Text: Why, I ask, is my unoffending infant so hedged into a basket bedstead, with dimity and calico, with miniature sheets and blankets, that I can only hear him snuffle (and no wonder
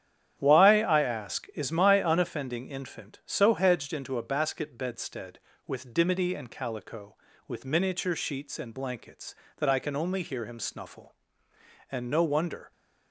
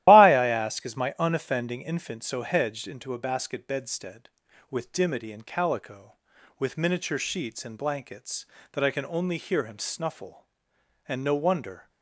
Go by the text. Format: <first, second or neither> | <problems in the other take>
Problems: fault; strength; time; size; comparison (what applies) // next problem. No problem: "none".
first | loses the start of "Why"; at 0.0 s; 125 ms // starts louder than the rest; strong; until 1.0 s; 14 dB; strong in the first